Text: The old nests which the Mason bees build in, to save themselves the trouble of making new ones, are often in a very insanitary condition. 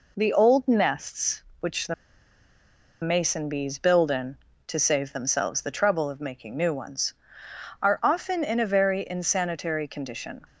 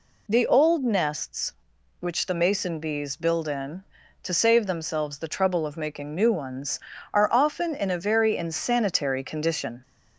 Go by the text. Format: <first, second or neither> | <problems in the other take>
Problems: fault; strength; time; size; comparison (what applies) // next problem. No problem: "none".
second | pauses between "the" and "Mason"; at 1.9 s; 1.0 s long